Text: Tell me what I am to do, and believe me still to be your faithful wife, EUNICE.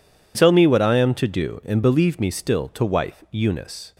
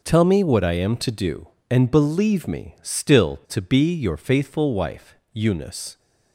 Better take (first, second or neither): second